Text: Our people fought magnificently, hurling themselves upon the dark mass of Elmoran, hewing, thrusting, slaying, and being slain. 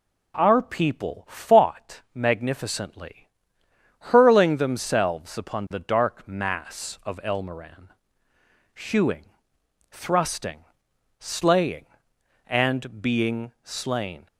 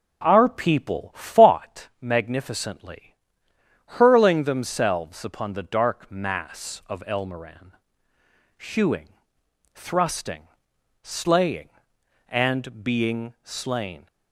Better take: first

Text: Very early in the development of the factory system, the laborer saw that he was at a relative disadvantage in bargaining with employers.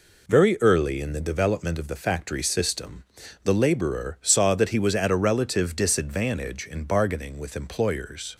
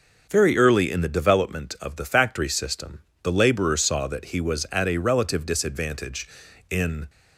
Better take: first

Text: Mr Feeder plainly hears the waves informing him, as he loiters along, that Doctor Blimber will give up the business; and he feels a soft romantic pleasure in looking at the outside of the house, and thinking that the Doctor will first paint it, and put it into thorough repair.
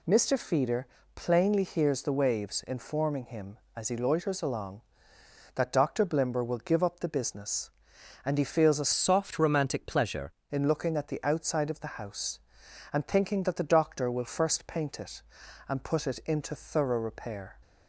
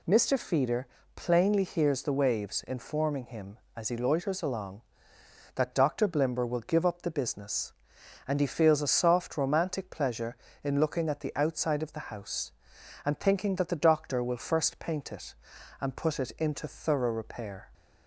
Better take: second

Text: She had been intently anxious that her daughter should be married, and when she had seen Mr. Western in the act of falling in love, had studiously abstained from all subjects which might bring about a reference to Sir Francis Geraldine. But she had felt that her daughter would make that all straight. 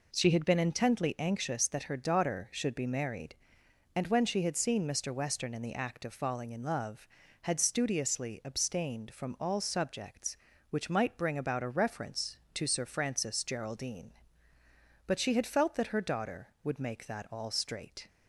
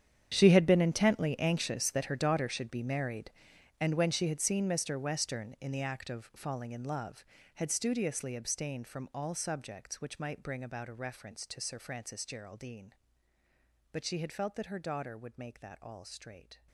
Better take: first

